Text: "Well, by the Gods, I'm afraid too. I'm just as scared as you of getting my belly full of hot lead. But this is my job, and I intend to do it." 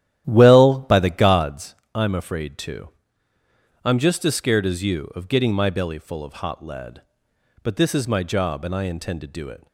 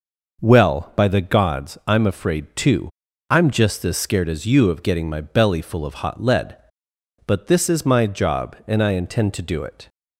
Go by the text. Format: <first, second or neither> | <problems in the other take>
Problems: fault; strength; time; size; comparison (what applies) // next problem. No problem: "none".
second | starts louder than the rest; strong; until 1.6 s; 12 dB